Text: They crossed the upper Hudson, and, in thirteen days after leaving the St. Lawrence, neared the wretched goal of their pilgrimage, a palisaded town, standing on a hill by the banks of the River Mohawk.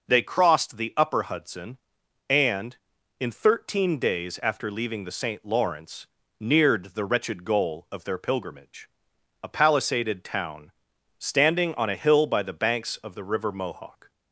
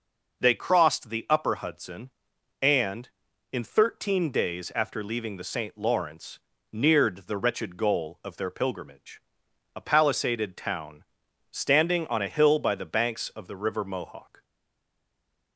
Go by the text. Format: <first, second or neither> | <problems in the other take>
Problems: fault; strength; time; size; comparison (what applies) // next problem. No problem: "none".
first | stays silent after the last word; from 14.4 s on; 1.1 s long